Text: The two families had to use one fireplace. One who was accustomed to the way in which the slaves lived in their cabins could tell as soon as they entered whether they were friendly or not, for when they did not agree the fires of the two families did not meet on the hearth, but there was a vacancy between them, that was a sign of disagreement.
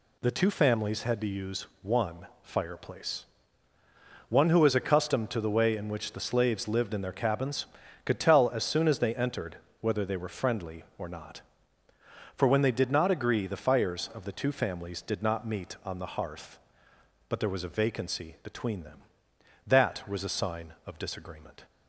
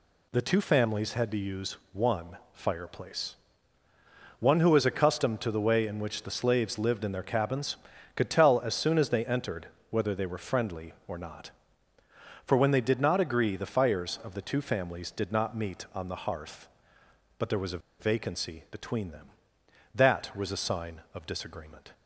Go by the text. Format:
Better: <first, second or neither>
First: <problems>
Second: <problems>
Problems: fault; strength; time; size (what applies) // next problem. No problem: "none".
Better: first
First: pauses between "use" and "one"; slight; at 1.6 s; 0.16 s long // pauses between "one" and "fireplace"; slight; at 2.2 s; 0.16 s long // pauses between "entered" and "whether"; slight; at 9.5 s; 0.21 s long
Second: pauses between "use" and "one"; slight; at 1.7 s; 0.16 s long // pauses between "one" and "fireplace"; slight; at 2.3 s; 0.16 s long // pauses between "entered" and "whether"; slight; at 9.6 s; 0.20 s long // pauses between "a" and "vacancy"; slight; at 17.7 s; 0.20 s long